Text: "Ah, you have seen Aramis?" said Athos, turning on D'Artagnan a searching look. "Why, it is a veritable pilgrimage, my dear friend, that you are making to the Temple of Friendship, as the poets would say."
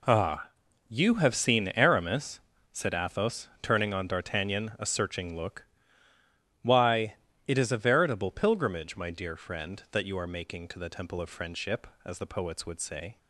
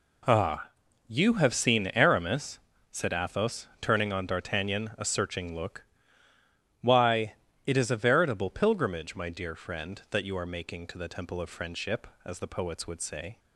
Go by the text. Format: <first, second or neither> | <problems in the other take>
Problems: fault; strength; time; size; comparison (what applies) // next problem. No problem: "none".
neither | none